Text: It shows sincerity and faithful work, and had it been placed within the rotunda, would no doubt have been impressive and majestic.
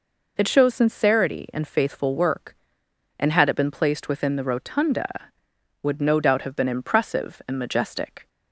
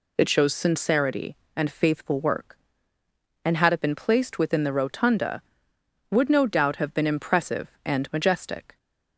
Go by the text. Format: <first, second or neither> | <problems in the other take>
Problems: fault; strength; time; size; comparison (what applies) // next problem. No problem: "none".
neither | none